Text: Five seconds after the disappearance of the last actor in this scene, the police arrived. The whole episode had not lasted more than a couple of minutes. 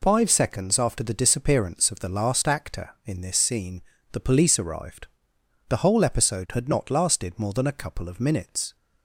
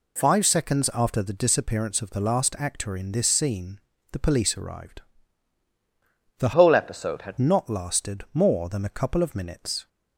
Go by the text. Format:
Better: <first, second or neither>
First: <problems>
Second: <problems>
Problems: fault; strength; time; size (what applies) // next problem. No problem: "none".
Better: first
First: none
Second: changes voice from "whole" to "had"; from 6.5 to 7.3 s; 0.8 s long